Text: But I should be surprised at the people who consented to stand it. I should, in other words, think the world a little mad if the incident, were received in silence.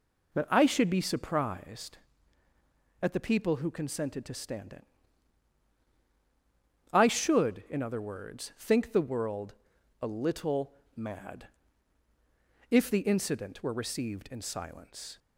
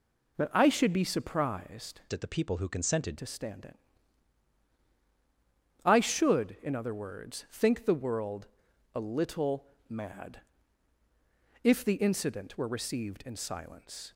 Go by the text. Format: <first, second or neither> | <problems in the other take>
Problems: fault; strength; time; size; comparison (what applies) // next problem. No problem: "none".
first | changes voice from "at" to "consented"; from 2.1 to 3.1 s; 1.0 s long // pauses between "world" and "a"; noticeable; at 8.4 s; 0.46 s long; noticeable in the first // pauses between "little" and "mad"; slight; at 9.6 s; 0.22 s long; slight in the first // pauses between "mad" and "if"; at 10.4 s; 1.2 s long; also in the first